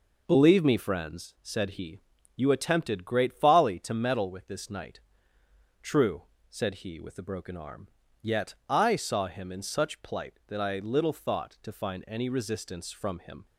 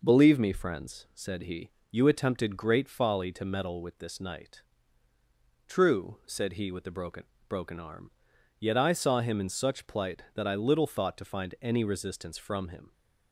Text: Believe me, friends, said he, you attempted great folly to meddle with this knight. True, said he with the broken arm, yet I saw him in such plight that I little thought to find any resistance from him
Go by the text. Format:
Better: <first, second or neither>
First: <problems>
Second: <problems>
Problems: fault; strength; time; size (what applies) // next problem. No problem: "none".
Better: first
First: none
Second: says "broken" twice; at 7.5 s